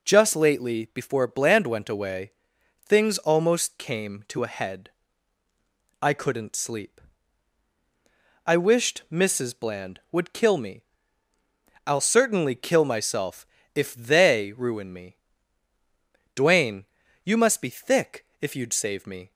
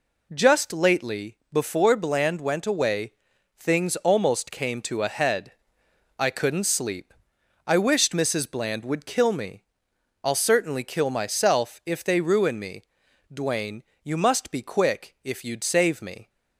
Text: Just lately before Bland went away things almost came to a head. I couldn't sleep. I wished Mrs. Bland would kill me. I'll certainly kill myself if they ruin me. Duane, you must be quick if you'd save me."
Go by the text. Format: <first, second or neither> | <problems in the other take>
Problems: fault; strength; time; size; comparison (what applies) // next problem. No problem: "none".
second | pauses between "away" and "things"; noticeable; at 2.3 s; 0.54 s long; noticeable in the second // pauses between "myself" and "if"; slight; at 13.4 s; 0.30 s long // says "thick" for "quick"; at 17.6 s